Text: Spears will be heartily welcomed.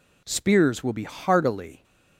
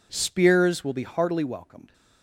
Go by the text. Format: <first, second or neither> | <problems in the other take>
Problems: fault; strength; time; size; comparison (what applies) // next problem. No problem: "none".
second | stops before "welcomed"; at 1.8 s